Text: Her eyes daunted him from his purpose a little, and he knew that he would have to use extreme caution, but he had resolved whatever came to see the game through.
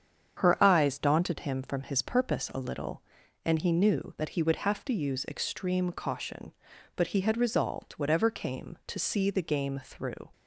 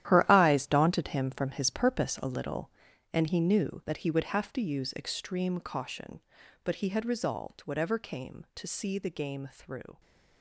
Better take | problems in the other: first | gets quieter; strong; throughout; 13 dB // starts louder than the rest; strong; until 1.1 s; 12 dB; strong in the first

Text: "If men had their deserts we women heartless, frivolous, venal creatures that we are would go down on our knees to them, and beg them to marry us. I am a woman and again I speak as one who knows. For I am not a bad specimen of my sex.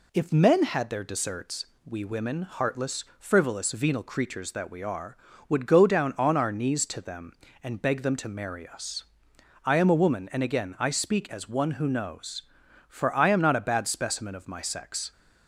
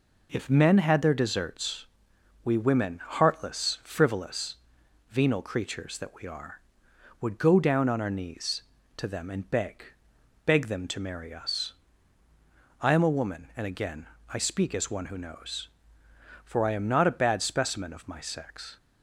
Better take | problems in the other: first | pauses between "deserts" and "we"; noticeable; at 1.8 s; 0.58 s long; slight in the first // says "beg" twice; at 10.4 s // pauses between "again" and "I"; slight; at 14.0 s; 0.26 s long

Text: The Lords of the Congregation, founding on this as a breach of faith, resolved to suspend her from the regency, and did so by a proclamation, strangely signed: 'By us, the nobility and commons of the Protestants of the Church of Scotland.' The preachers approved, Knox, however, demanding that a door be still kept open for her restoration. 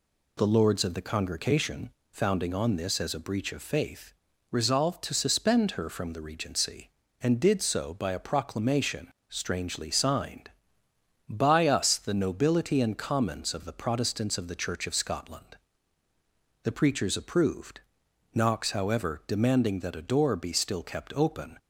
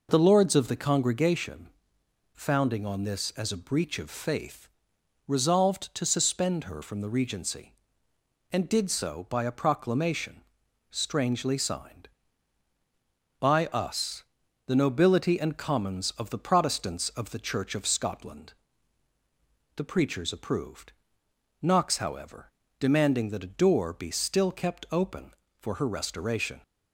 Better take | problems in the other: second | stops before "for her restoration"; at 21.5 s

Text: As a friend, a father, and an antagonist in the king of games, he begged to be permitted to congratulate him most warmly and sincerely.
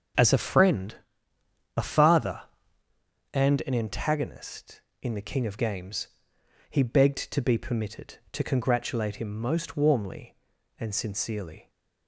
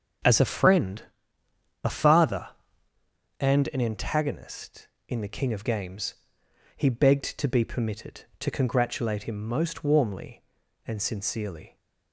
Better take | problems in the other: neither | starts louder than the rest; the same in both

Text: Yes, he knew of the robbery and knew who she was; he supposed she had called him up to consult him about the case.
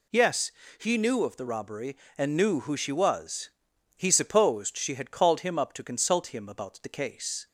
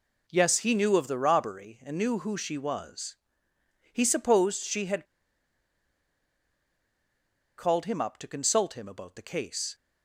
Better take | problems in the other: first | pauses between "had" and "called"; strong; at 5.0 s; 2.5 s long

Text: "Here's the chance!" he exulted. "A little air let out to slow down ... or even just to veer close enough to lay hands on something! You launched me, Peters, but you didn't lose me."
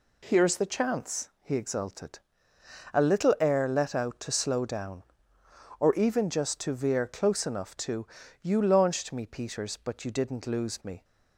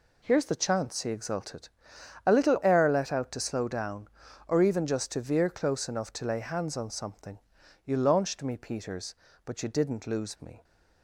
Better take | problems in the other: second | skips "lay hands on something"; at 8.2 s

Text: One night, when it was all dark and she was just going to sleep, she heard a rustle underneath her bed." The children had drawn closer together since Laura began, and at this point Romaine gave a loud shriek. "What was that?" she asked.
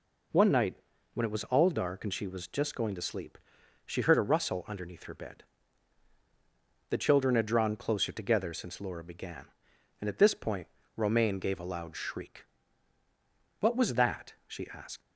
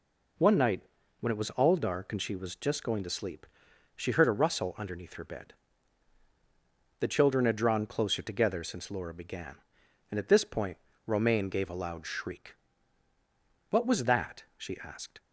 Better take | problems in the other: second | pauses between "point" and "Romaine"; slight; at 10.6 s; 0.28 s long; slight in the second // leaves "asked" unfinished; at 15.0 s; 70 ms

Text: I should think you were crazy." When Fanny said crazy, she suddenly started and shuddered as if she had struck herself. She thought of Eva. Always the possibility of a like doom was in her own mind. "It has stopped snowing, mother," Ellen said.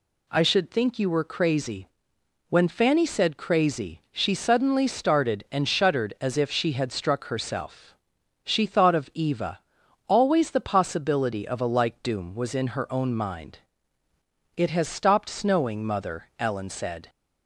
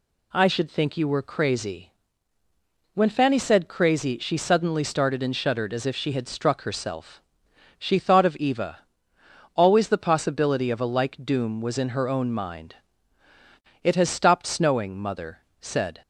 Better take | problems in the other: first | skips "Ellen"; at 15.4 s

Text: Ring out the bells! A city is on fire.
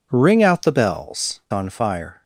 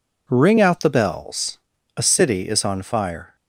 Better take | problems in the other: second | skips "A city is"; at 1.4 s

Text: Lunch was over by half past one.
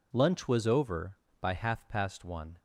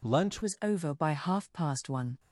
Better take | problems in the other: first | changes voice at "was"; from 0.4 s on; 1.7 s long

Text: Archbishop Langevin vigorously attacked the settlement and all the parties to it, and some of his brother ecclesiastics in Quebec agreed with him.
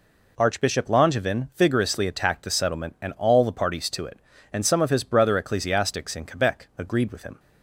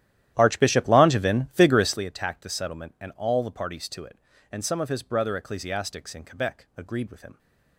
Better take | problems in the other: first | starts louder than the rest; strong; until 2.0 s; 12.5 dB

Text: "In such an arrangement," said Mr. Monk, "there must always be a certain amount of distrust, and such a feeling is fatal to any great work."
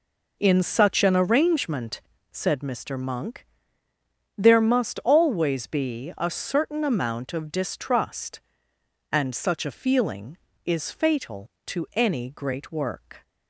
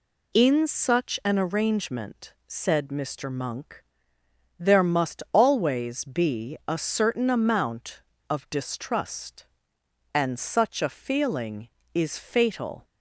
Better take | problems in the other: first | stops before "to any great work"; at 12.8 s

